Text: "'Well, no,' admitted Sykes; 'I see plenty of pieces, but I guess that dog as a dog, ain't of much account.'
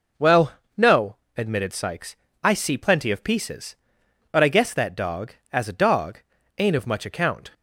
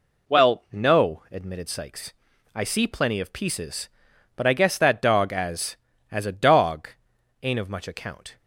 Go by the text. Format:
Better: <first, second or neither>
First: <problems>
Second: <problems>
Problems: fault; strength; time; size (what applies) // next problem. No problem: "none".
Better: first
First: none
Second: says "as" twice; at 6.1 s